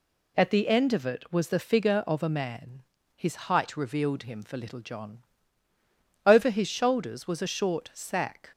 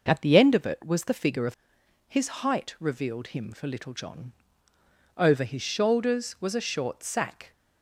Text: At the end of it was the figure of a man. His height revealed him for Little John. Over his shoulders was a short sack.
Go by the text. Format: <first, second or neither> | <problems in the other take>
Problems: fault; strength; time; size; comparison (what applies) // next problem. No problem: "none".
first | skips "a man"; at 1.8 s